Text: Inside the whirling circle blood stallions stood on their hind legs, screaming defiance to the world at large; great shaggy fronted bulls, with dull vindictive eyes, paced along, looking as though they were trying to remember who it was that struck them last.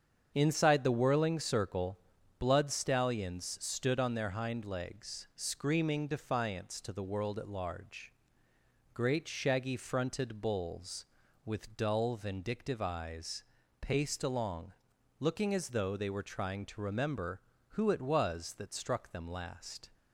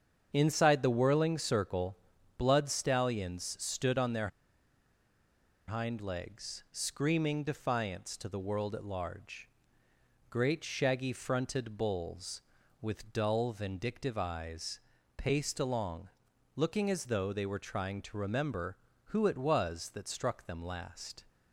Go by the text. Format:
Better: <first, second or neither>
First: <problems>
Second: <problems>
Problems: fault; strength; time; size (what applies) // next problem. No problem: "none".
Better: first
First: starts louder than the rest; strong; until 1.3 s; 7.5 dB // pauses between "circle" and "blood"; at 1.9 s; 0.40 s long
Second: starts louder than the rest; strong; until 1.3 s; 7.5 dB // pauses between "circle" and "blood"; at 1.9 s; 0.40 s long // pauses between "their" and "hind"; strong; at 4.2 s; 1.3 s long